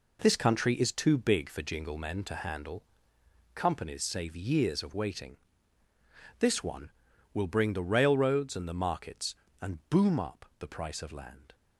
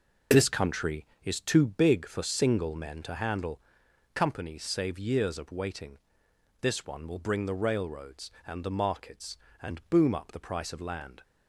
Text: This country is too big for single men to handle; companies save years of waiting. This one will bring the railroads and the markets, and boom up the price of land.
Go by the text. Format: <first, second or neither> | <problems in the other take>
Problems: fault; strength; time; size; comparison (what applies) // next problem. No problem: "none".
second | says "jingle" for "single"; at 1.6 s